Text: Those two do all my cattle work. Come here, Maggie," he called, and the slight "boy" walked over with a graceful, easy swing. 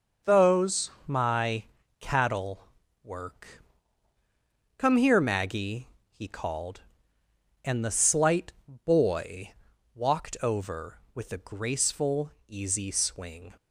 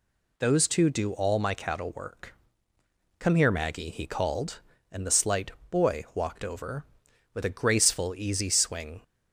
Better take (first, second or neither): second